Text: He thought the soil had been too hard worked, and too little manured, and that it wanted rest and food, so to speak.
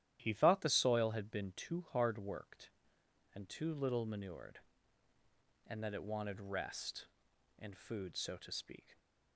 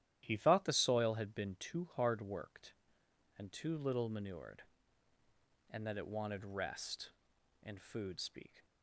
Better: first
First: starts louder than the rest; strong; until 1.2 s; 12.5 dB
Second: starts louder than the rest; strong; until 1.2 s; 12.5 dB // skips "so to"; at 8.1 s

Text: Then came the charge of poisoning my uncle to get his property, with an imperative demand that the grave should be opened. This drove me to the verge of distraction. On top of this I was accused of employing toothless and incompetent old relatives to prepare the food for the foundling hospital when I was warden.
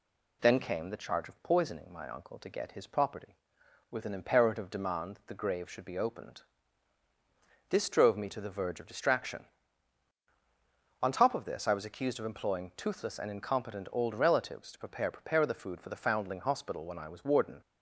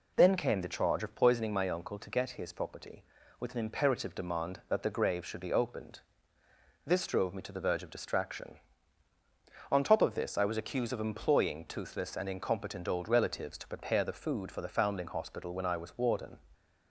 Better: second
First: says "prepare" twice; at 15.1 s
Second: none

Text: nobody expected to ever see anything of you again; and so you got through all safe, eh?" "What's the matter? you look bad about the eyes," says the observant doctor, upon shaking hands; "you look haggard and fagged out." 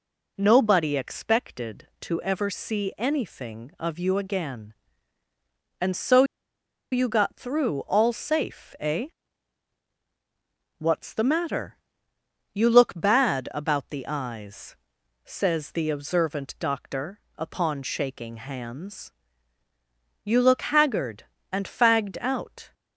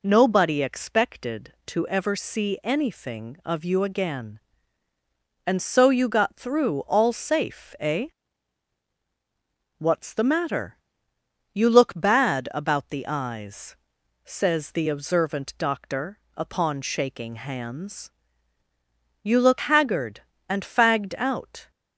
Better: second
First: pauses between "so" and "you"; noticeable; at 6.2 s; 0.68 s long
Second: none

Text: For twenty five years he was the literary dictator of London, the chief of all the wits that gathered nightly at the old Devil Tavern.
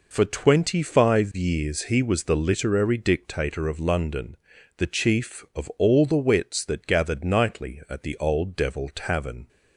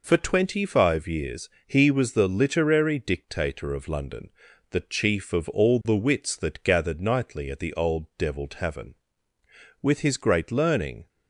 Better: first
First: none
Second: pauses between "years" and "he"; slight; at 1.4 s; 0.18 s long // goes on to say "With his great learning"; noticeable; from 9.8 s on; 1.2 s long

